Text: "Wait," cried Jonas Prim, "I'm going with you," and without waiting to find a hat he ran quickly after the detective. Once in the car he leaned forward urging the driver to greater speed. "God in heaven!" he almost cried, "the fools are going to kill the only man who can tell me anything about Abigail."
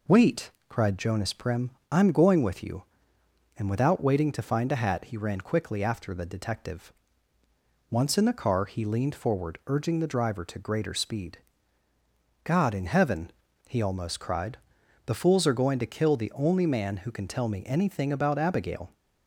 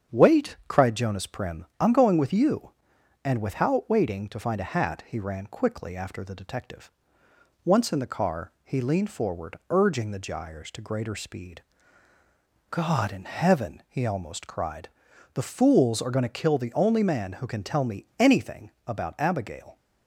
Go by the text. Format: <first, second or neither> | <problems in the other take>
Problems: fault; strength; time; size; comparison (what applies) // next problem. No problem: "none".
first | starts louder than the rest; strong; until 1.2 s; 7.5 dB // says "gyres" for "driver"; at 10.1 s // pauses between "anything" and "about"; slight; at 18.7 s; 0.16 s long